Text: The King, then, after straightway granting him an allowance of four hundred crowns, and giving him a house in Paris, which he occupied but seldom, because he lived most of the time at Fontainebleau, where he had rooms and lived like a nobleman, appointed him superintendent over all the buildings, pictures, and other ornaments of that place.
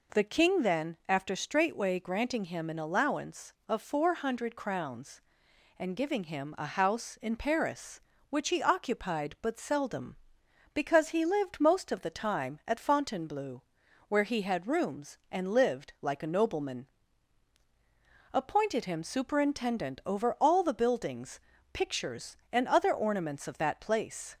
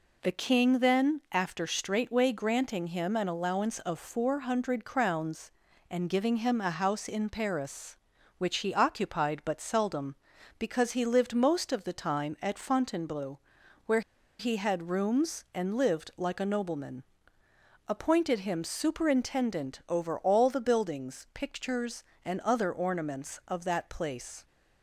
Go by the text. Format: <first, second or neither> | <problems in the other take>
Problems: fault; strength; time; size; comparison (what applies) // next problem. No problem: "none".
first | pauses between "where" and "he"; at 14.0 s; 0.39 s long